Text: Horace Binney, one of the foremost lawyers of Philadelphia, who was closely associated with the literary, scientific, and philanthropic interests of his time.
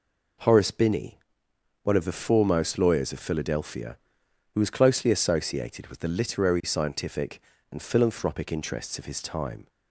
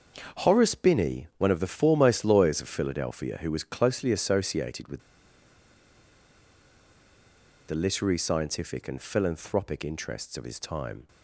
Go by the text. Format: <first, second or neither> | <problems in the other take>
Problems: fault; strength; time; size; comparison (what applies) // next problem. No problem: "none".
first | starts louder than the rest; until 1.4 s; 6.5 dB // pauses between "with" and "the"; strong; at 4.9 s; 2.6 s long